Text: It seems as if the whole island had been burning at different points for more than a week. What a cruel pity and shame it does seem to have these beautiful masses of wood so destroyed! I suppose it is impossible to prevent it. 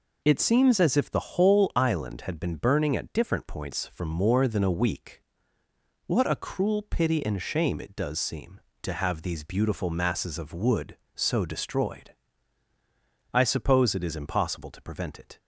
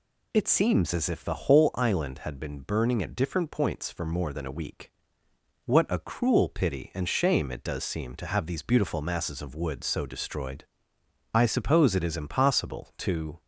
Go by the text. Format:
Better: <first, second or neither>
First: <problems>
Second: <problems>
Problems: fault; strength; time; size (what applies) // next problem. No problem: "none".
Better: first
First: none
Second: stops before "prevent it"; at 13.3 s